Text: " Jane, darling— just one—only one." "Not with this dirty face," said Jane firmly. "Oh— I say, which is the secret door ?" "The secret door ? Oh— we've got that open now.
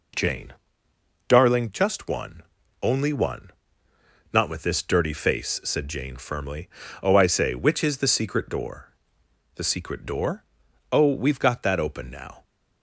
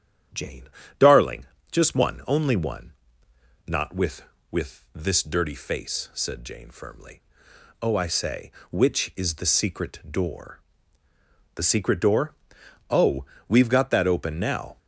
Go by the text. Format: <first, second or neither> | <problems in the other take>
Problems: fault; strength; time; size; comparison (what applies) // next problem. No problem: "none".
first | starts louder than the rest; strong; until 1.8 s; 10 dB // says "with" twice; at 4.4 s